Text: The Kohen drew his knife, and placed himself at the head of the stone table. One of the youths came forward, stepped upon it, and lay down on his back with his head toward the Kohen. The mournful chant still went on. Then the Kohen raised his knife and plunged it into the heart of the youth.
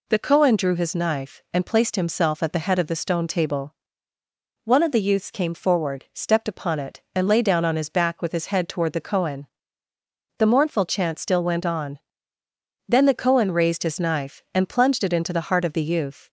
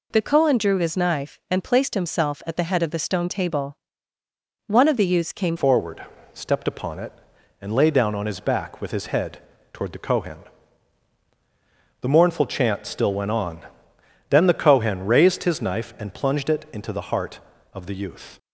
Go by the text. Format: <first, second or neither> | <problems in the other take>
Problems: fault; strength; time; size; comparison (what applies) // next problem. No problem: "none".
first | changes voice at "forward"; from 5.5 s on; 12.8 s long // pauses between "head" and "toward"; slight; at 9.3 s; 0.34 s long